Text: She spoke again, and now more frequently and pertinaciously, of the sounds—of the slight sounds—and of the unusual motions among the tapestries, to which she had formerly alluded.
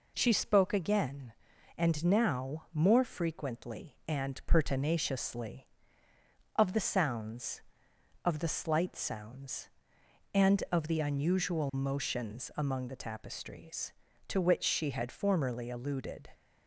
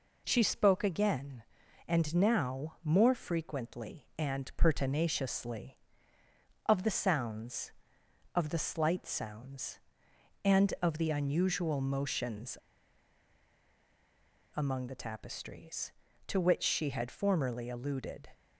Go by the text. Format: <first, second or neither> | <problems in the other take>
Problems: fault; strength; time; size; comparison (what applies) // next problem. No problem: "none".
first | pauses between "motions" and "among"; strong; at 12.5 s; 1.9 s long